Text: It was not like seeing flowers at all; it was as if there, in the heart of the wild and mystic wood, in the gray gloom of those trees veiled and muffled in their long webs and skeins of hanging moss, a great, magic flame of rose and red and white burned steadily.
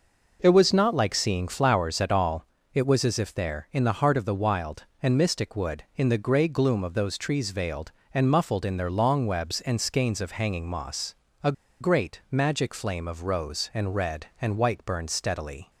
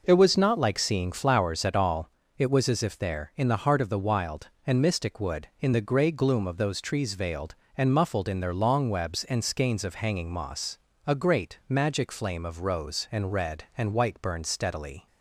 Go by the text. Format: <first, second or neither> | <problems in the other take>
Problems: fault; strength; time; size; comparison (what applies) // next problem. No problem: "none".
second | pauses between "a" and "great"; slight; at 11.5 s; 0.28 s long